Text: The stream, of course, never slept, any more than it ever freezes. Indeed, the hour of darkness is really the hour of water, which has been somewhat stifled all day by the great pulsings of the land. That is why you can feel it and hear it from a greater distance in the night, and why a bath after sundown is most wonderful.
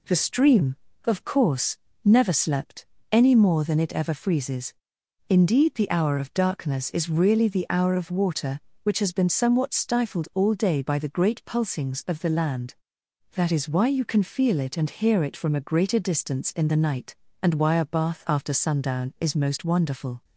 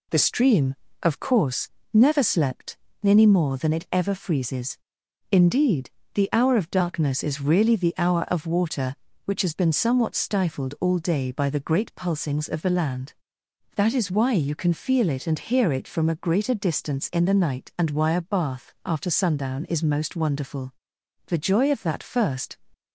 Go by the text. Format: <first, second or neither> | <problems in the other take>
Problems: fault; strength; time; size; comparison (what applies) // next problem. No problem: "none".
first | goes on to say "The joy of that first"; from 21.2 s on; 1.3 s long